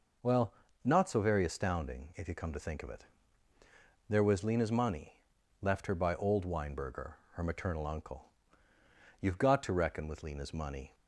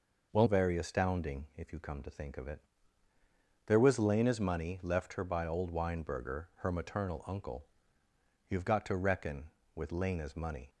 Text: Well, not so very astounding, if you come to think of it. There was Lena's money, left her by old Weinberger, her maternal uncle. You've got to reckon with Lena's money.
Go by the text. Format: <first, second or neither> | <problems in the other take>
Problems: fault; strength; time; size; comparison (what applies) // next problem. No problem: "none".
first | skips "not so"; at 0.4 s